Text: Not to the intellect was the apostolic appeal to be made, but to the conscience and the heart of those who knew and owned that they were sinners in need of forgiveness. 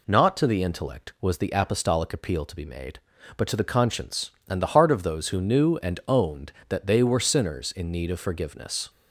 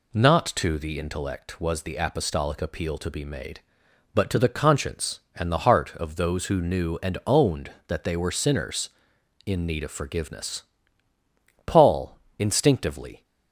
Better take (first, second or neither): first